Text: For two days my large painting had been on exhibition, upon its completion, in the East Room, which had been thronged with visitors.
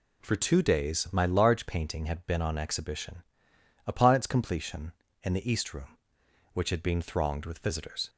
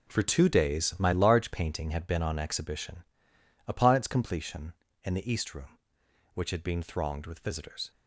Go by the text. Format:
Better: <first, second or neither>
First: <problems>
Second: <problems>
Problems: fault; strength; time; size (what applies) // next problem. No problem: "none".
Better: first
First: none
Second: gets quieter; strong; throughout; 11 dB